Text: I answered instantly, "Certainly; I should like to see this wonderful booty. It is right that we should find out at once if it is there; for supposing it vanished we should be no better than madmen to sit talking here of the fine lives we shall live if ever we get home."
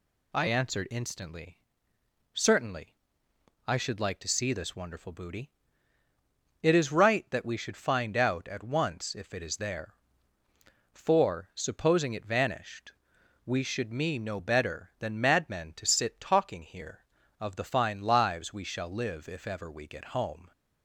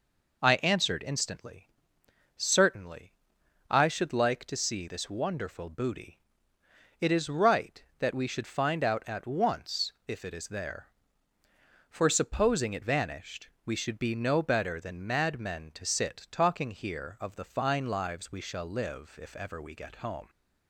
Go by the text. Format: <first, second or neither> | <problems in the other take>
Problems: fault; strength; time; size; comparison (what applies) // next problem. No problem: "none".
second | pauses between "vanished" and "we"; noticeable; at 12.9 s; 0.54 s long; slight in the second // says "me" for "be"; at 13.8 s